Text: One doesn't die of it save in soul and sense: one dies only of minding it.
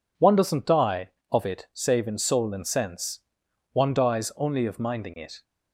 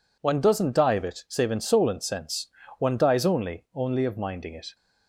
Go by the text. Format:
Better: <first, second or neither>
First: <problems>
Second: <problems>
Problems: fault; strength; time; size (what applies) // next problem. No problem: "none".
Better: first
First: none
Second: says "only" twice; at 3.7 s